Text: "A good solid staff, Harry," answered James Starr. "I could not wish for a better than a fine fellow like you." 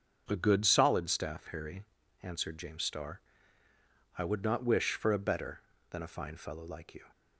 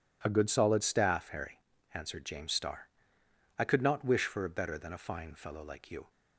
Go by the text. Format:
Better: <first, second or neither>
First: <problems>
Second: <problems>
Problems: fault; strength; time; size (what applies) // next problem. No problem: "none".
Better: second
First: starts louder than the rest; until 1.2 s; 7 dB // says "would" for "could"; at 4.2 s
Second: none